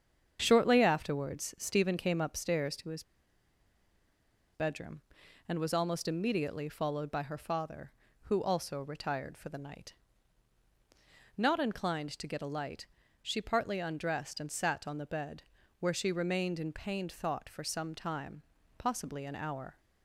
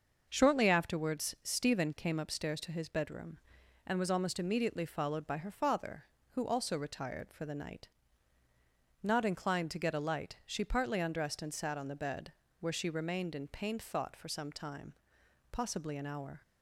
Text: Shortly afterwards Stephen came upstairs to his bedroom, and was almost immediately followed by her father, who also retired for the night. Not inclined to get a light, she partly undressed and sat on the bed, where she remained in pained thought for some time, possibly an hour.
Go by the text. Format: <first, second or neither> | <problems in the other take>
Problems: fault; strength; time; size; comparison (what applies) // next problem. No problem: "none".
second | starts louder than the rest; strong; until 1.4 s; 7.5 dB; also in the second // pauses between "his" and "bedroom"; strong; at 3.0 s; 1.5 s long